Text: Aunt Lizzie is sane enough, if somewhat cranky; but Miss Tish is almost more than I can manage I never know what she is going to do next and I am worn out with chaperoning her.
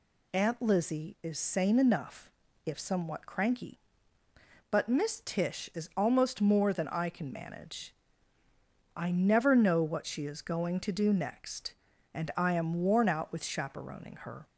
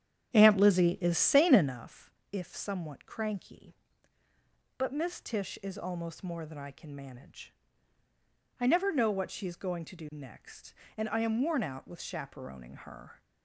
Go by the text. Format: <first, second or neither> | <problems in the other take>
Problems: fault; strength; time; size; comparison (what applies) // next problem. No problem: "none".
first | starts louder than the rest; strong; until 1.8 s; 10 dB // pauses between "manage" and "I"; at 7.5 s; 1.0 s long; also in the first